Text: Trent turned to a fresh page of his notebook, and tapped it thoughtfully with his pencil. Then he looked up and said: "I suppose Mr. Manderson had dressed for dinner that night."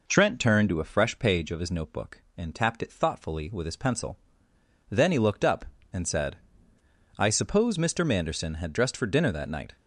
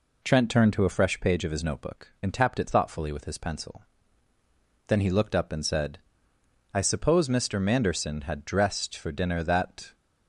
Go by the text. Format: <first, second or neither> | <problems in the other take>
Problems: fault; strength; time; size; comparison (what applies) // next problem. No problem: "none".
first | stops before "night"; at 9.9 s